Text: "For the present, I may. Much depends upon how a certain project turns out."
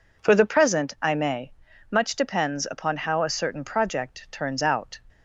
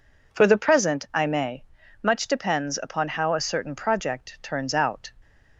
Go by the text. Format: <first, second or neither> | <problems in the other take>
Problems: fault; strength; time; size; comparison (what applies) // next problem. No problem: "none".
neither | none